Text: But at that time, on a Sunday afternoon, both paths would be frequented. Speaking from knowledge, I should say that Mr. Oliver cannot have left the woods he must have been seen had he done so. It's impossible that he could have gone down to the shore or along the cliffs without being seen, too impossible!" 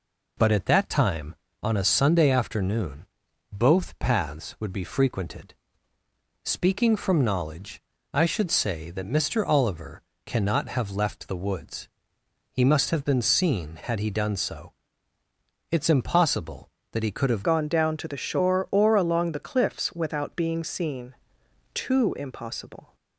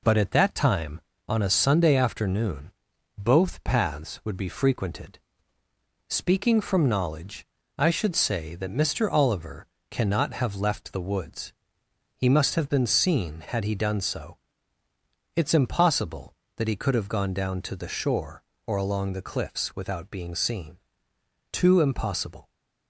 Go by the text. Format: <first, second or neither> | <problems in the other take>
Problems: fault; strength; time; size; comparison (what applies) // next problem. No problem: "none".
second | pauses between "Oliver" and "cannot"; slight; at 10.0 s; 0.26 s long; slight in the second // pauses between "woods" and "he"; noticeable; at 11.8 s; 0.64 s long; noticeable in the second // changes voice at "gone"; from 17.4 s on; 5.5 s long